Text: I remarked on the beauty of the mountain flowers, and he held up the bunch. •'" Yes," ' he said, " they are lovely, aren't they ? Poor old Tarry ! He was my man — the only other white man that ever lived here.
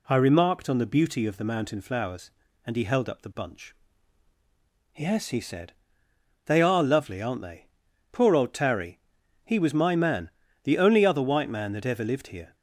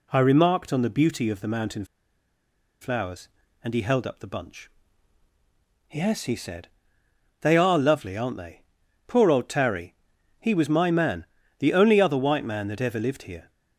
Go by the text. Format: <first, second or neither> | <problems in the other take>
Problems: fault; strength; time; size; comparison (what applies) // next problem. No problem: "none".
first | pauses between "mountain" and "flowers"; noticeable; at 1.8 s; 0.97 s long